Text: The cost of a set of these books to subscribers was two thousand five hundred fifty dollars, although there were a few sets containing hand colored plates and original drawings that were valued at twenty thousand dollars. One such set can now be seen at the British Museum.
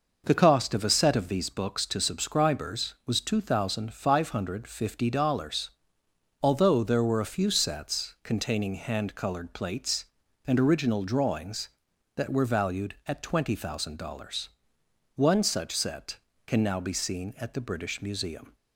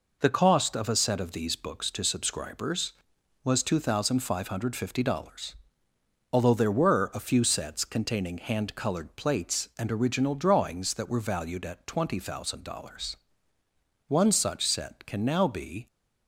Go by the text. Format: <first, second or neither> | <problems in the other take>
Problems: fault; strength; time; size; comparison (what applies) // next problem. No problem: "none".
first | stops before "seen at the British Museum"; at 15.8 s